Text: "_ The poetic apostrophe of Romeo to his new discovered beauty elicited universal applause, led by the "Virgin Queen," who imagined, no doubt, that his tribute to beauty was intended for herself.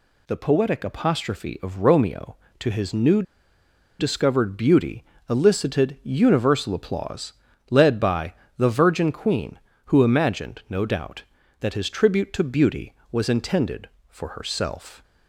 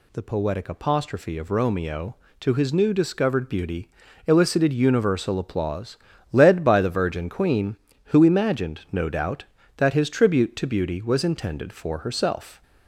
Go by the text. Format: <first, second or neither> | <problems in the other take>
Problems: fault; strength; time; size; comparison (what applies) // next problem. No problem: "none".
second | pauses between "new" and "discovered"; noticeable; at 3.2 s; 0.77 s long // pauses between "beauty" and "elicited"; slight; at 5.0 s; 0.28 s long; slight in the second // pauses between "by" and "the"; slight; at 8.3 s; 0.24 s long